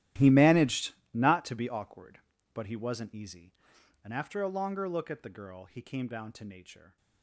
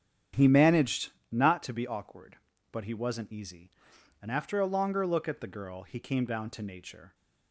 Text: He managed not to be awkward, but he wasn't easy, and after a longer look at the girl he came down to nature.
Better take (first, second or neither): second